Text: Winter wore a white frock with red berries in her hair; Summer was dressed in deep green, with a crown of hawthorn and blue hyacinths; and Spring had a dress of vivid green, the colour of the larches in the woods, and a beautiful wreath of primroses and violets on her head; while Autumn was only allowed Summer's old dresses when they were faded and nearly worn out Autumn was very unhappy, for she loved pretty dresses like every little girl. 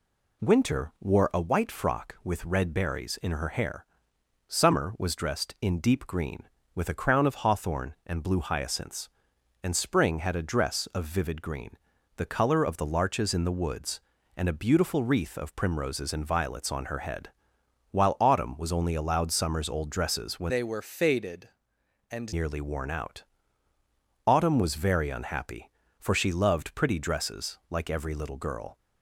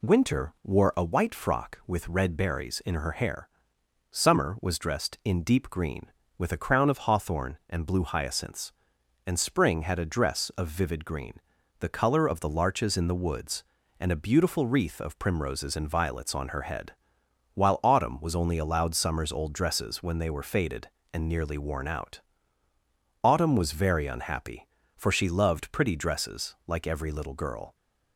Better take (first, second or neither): second